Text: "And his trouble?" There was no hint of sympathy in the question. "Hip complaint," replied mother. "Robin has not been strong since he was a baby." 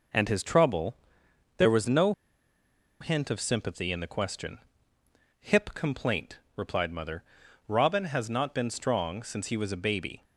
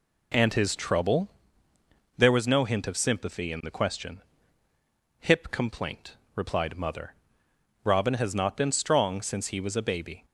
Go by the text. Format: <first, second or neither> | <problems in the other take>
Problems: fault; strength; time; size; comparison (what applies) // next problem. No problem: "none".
second | pauses between "no" and "hint"; noticeable; at 2.1 s; 0.89 s long